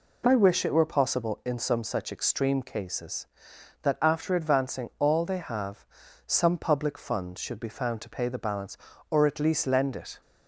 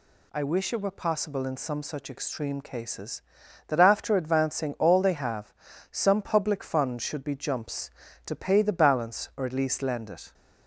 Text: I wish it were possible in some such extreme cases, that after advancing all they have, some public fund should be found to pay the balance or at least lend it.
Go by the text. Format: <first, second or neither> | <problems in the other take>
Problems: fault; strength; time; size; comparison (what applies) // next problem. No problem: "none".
first | says "jumps" for "found"; at 7.3 s